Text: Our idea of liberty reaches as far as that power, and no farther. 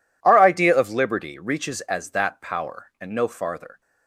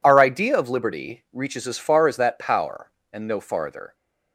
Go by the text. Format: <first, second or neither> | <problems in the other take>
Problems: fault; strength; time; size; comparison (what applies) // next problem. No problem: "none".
second | skips "far as"; at 2.1 s